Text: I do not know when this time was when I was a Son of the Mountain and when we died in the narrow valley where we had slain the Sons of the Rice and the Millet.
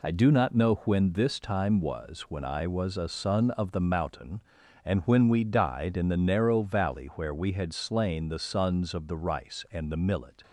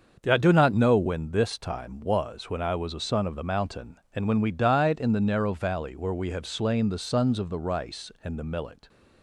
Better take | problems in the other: first | starts louder than the rest; until 1.2 s; 6.5 dB // says "have" for "had"; at 6.3 s

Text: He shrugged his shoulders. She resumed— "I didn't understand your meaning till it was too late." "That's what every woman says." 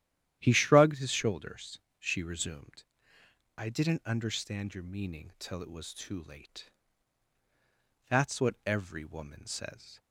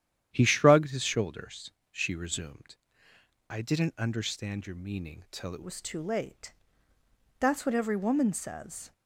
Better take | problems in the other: first | starts louder than the rest; strong; until 1.3 s; 10.5 dB; strong in the first // changes voice at "was"; from 5.6 s on; 3.3 s long

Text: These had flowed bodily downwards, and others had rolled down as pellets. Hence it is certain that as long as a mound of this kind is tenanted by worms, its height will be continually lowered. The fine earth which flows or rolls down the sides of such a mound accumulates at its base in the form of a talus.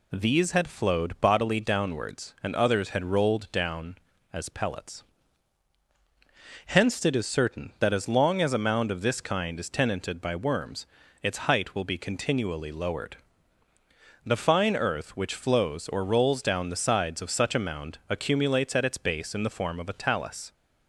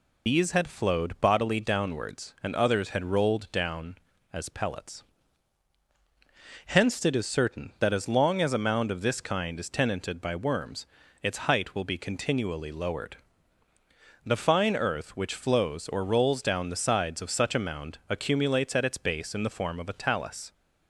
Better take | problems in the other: first | loses the start of "These"; at 0.2 s; 140 ms

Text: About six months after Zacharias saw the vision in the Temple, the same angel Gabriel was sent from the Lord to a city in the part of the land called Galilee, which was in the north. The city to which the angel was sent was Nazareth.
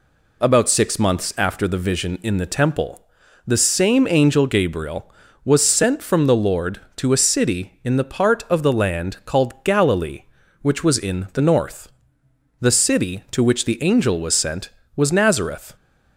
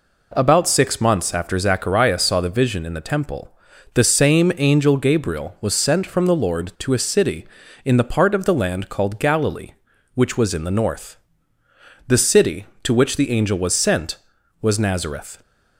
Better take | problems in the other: second | skips "Zacharias saw"; at 1.6 s

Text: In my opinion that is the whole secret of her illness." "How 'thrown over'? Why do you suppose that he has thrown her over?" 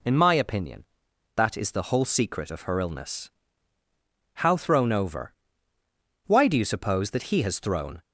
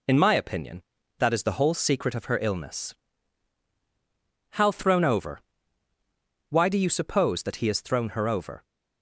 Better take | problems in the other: second | stops before "her over"; at 8.0 s

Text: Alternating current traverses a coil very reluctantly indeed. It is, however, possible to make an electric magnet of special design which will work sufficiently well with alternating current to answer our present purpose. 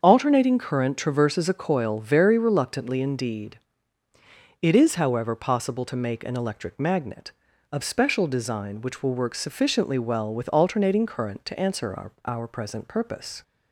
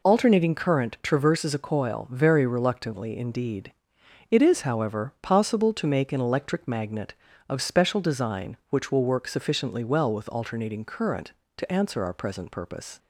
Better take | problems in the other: second | starts louder than the rest; until 1.0 s; 7 dB // says "our" twice; at 12.2 s

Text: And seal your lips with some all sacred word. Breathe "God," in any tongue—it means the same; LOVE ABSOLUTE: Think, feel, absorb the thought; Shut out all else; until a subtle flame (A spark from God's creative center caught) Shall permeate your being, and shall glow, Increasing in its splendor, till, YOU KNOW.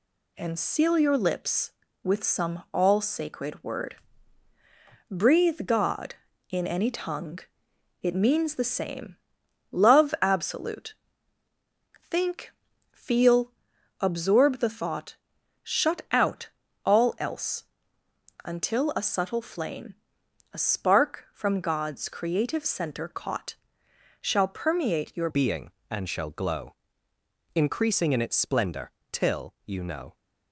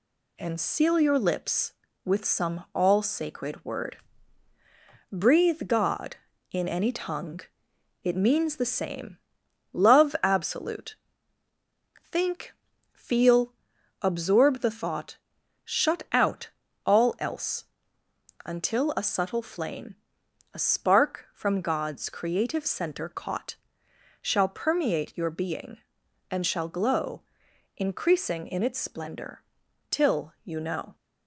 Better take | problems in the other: second | pauses between "out" and "all"; slight; at 16.4 s; 0.34 s long; slight in the second // changes voice at "being"; from 25.2 s on; 4.9 s long

